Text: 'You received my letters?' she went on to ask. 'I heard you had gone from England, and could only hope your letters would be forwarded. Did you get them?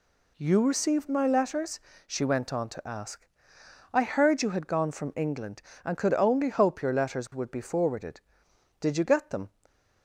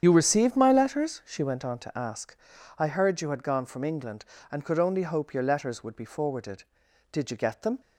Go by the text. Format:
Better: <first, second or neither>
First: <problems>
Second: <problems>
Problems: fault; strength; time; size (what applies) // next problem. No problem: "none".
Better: first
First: none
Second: loses the start of "You"; at 0.0 s; 50 ms // starts louder than the rest; strong; until 1.0 s; 8.5 dB